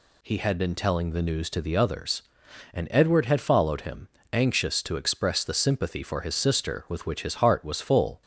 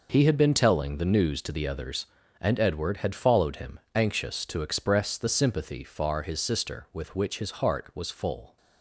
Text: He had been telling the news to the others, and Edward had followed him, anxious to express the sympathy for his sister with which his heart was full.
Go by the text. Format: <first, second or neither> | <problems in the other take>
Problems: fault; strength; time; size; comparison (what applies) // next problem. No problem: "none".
first | says "far" for "for"; at 5.8 s